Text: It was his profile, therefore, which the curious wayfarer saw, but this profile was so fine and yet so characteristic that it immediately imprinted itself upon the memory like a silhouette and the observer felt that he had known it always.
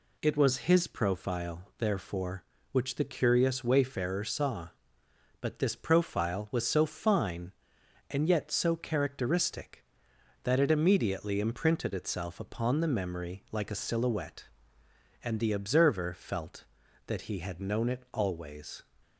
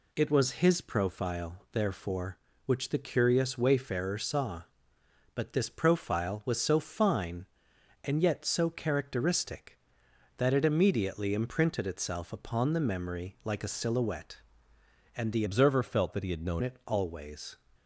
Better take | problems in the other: first | changes voice from "observer" to "known"; from 15.4 to 16.6 s; 1.2 s long

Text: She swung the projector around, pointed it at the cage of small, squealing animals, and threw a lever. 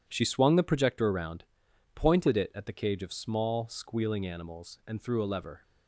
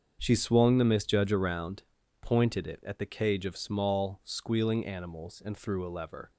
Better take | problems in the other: first | starts louder than the rest; strong; until 1.2 s; 7 dB // says "misjudge" for "projector"; at 0.8 s

